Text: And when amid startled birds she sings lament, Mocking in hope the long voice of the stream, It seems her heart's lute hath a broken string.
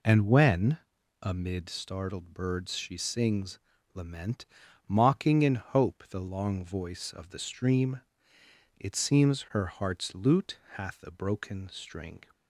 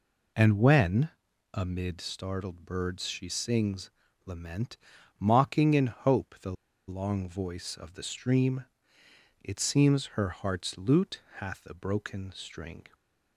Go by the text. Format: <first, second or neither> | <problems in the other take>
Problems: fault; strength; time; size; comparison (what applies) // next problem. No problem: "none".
first | pauses between "when" and "amid"; at 1.0 s; 0.44 s long; also in the first // pauses between "sings" and "lament"; slight; at 3.9 s; 0.34 s long; slight in the first // pauses between "the" and "long"; slight; at 6.5 s; 0.35 s long // pauses between "lute" and "hath"; slight; at 11.2 s; 0.16 s long; slight in the first